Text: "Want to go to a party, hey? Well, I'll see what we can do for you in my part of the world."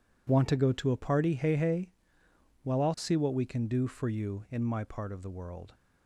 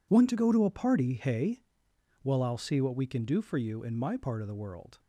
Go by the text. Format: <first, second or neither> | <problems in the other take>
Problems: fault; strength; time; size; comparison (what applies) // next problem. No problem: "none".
second | says "hey" twice; at 1.5 s